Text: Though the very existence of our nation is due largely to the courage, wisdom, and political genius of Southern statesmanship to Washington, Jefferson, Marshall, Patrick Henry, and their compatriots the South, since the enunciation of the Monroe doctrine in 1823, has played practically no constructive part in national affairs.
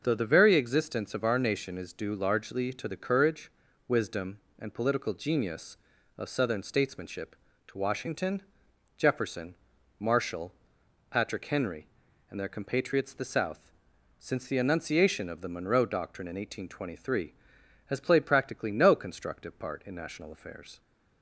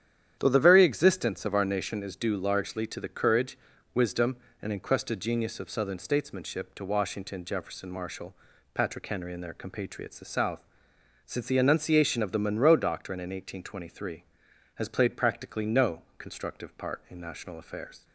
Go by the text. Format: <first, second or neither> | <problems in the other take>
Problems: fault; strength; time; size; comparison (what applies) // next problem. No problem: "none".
first | starts louder than the rest; strong; until 1.3 s; 10 dB // says "encrusted" for "political"; at 4.7 s // pauses between "no" and "constructive"; slight; at 16.0 s; 0.16 s long